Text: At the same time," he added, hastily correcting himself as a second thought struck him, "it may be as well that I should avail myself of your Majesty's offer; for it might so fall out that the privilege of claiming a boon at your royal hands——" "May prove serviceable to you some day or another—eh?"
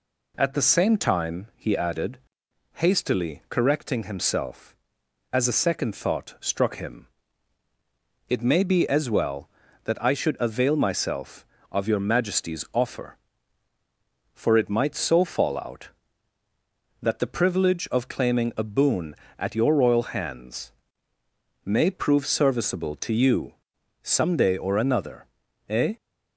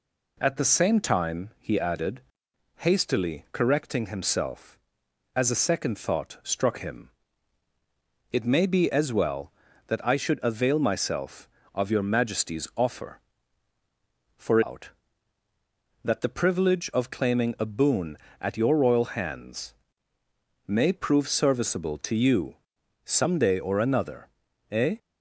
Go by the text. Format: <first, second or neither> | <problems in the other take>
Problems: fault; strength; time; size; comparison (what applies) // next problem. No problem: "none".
first | skips "it might so fall"; at 14.6 s // pauses between "you" and "some"; noticeable; at 22.5 s; 0.48 s long; noticeable in the first